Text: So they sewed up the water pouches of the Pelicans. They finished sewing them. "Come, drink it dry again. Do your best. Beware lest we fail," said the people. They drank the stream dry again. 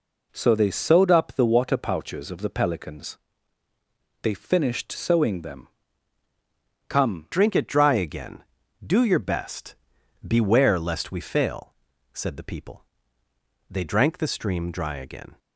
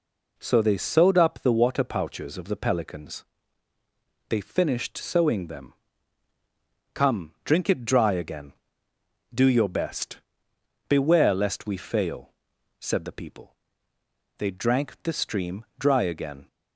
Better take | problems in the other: second | changes voice at "drink"; from 7.3 s on; 8.0 s long

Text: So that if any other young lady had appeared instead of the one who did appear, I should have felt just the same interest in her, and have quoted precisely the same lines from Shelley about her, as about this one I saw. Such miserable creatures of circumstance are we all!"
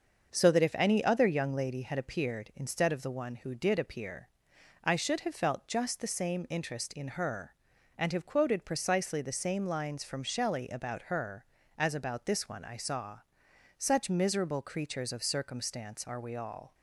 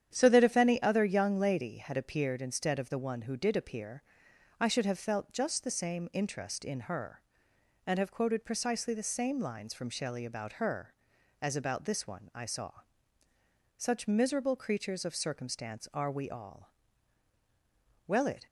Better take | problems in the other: first | starts louder than the rest; strong; until 1.1 s; 9.5 dB; also in the first // goes on to say "Well it"; slight; from 18.0 s on; 0.40 s long

